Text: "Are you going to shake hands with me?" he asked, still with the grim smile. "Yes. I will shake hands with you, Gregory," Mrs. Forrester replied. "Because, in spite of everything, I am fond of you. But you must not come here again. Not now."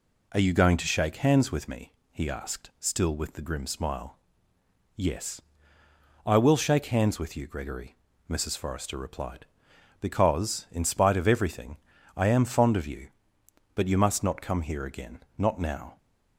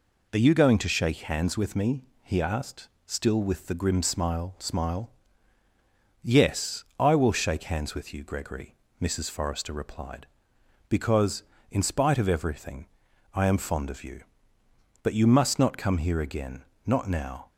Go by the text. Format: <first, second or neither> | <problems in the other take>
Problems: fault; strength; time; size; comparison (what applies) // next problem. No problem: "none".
first | says "smile" twice; at 4.5 s